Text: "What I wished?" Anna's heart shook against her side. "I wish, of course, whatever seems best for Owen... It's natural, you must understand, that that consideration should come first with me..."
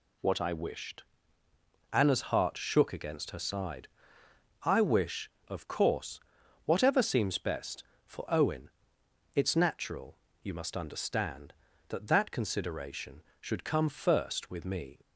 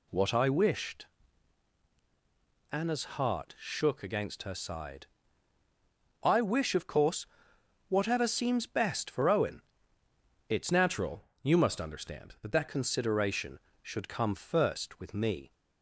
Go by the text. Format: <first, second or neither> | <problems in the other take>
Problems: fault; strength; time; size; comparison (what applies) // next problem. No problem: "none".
first | changes voice from "natural" to "that"; from 10.7 to 12.6 s; 1.9 s long